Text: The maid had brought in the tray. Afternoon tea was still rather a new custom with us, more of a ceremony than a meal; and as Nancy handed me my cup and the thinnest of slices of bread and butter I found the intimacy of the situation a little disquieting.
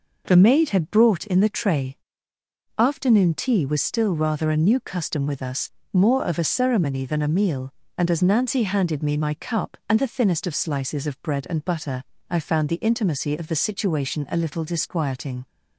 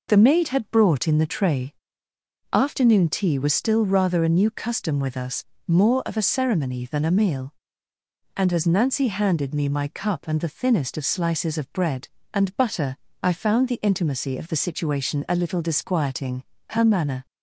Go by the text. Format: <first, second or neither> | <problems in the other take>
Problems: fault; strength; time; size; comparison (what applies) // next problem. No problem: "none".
first | pauses between "butter" and "I"; slight; at 12.9 s; 0.24 s long; slight in the first // goes on to say "Her manner"; from 16.6 s on; 0.56 s long